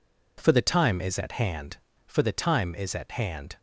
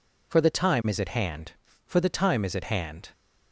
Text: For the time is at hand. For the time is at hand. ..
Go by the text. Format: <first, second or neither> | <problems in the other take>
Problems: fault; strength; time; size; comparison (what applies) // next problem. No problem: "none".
neither | none